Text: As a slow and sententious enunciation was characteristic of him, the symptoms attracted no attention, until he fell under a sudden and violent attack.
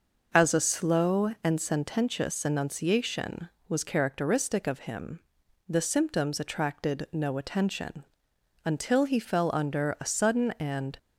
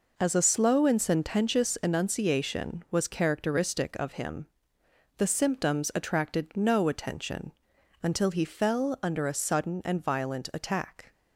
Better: second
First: stops before "violent attack"; at 10.9 s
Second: none

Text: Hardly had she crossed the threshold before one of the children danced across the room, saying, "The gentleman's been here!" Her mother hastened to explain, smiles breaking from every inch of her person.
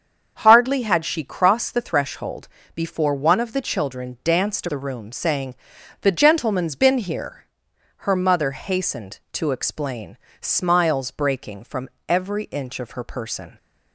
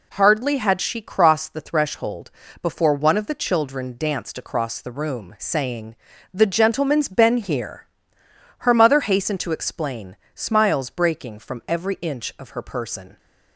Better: second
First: starts louder than the rest; until 1.3 s; 7 dB // pauses between "threshold" and "before"; slight; at 2.4 s; 0.26 s long // skips "across"; at 4.6 s // pauses between "from" and "every"; slight; at 11.8 s; 0.18 s long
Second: pauses between "threshold" and "before"; slight; at 2.3 s; 0.32 s long

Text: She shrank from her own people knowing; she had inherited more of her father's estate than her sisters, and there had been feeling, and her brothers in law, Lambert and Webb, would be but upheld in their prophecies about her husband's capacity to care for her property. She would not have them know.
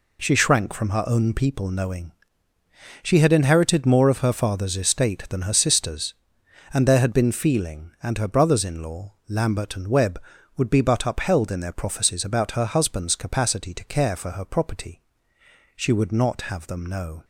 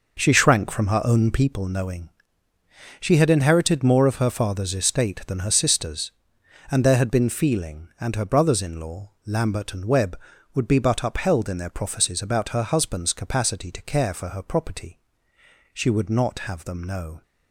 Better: first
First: none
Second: starts louder than the rest; noticeable; until 1.6 s; 5.5 dB

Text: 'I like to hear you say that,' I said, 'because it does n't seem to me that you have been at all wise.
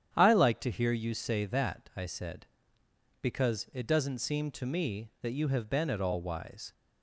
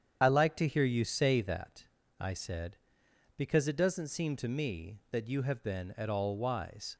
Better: first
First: starts louder than the rest; strong; until 1.1 s; 9.5 dB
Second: loses the start of "I"; at 0.2 s; 70 ms // starts louder than the rest; strong; until 1.2 s; 8.5 dB

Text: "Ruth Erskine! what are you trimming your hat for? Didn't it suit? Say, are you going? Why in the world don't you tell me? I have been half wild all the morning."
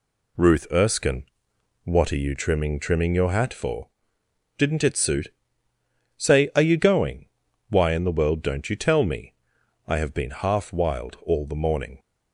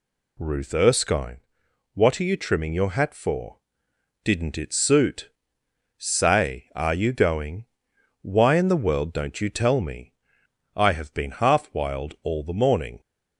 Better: second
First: says "trimming" twice; at 2.7 s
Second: none

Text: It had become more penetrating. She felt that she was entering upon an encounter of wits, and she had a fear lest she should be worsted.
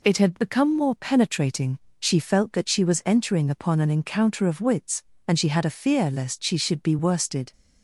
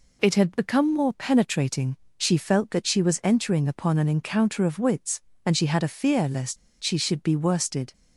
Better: first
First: none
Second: pauses between "lest" and "she"; slight; at 6.5 s; 0.25 s long

